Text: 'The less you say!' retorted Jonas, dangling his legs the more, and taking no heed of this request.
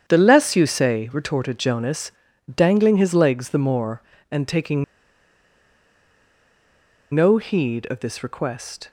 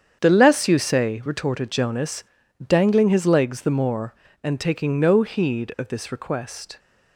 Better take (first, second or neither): second